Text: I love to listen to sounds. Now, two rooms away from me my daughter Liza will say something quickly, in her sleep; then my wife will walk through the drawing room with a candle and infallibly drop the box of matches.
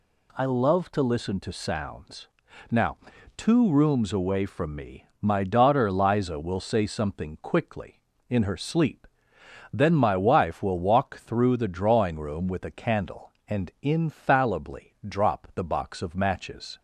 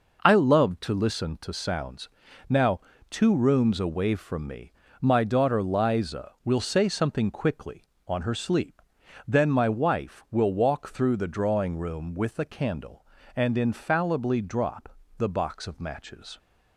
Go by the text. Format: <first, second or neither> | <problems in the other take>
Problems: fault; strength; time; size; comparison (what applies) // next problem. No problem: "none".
first | pauses between "me" and "my"; slight; at 4.7 s; 0.30 s long; slight in the first // says "on" for "in"; at 8.0 s // pauses between "drop" and "the"; slight; at 14.9 s; 0.22 s long